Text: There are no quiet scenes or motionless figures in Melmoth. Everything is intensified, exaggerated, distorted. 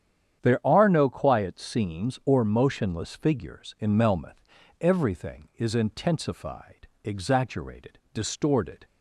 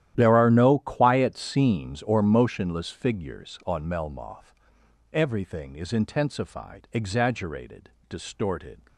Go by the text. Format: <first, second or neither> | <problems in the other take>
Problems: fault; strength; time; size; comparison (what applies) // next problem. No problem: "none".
first | starts louder than the rest; strong; until 1.1 s; 12 dB; strong in the first // says "on" for "in"; at 3.6 s